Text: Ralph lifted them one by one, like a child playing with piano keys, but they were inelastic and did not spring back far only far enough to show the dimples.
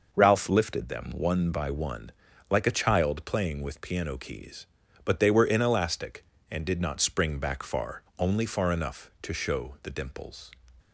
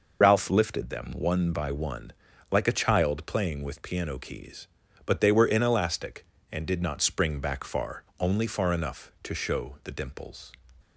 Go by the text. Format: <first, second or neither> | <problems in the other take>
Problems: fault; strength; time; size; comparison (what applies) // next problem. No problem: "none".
first | loses the start of "Ralph"; at 0.2 s; 60 ms // pauses between "far" and "only"; slight; at 8.0 s; 0.18 s long; slight in the first